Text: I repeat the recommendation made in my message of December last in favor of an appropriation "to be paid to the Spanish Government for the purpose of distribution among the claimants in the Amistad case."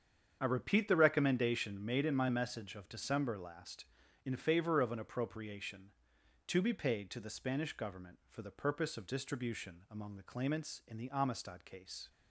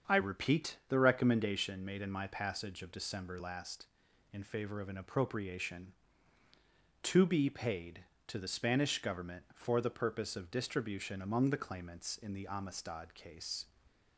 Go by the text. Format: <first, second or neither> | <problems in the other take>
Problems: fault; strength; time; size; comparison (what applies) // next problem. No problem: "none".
first | starts louder than the rest; strong; until 1.2 s; 7 dB; strong in the first // says "passage" for "message"; at 2.2 s